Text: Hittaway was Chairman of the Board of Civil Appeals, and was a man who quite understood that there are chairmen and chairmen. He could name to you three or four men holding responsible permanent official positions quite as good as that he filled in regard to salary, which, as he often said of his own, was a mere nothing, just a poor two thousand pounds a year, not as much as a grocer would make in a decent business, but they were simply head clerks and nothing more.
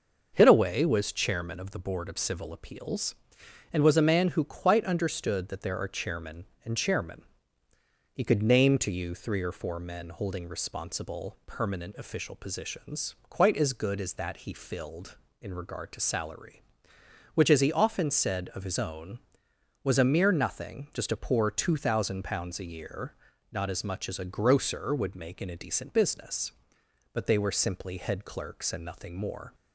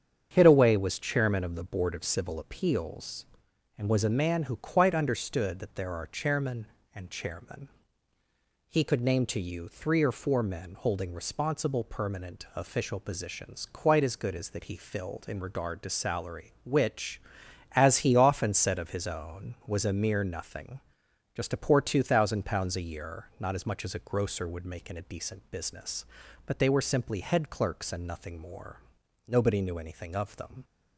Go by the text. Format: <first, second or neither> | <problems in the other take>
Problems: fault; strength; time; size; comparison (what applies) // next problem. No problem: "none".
first | starts louder than the rest; strong; until 1.3 s; 8 dB // goes on to say "Nobody knew anything of them"; from 29.2 s on; 1.3 s long